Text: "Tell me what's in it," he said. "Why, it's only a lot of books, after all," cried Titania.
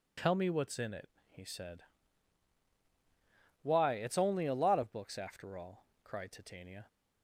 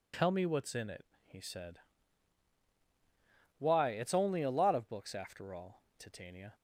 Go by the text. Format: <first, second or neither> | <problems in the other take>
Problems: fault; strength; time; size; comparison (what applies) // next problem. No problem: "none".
first | skips "cried"; at 5.9 s